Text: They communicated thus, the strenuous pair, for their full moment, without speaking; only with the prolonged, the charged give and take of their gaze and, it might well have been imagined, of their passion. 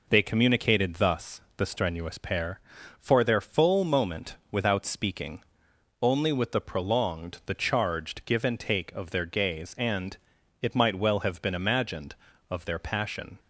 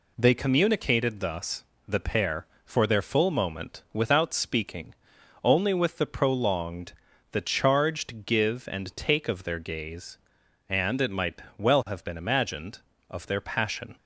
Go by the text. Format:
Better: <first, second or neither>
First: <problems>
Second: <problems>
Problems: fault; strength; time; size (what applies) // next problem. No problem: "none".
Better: first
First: none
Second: skips "strenuous"; at 1.9 s // pauses between "might" and "well"; slight; at 11.4 s; 0.16 s long